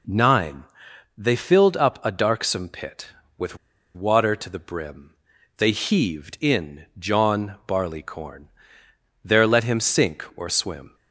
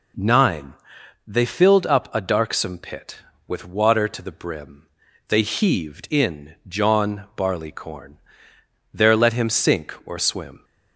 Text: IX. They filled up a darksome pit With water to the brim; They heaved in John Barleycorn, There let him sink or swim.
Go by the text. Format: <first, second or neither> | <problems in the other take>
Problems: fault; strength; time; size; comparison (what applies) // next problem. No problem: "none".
second | pauses between "With" and "water"; at 3.5 s; 0.37 s long